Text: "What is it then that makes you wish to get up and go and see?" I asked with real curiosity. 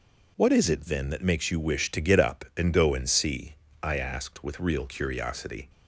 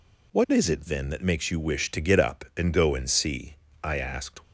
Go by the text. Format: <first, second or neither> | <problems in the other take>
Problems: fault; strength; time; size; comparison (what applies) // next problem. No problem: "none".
first | stops before "with real curiosity"; at 4.4 s